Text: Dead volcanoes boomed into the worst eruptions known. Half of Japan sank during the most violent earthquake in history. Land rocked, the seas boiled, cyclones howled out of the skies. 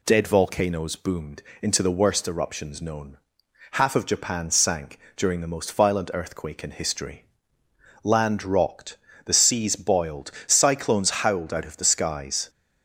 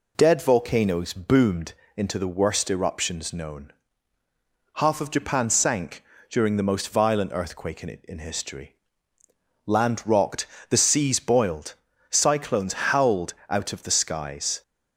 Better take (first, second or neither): first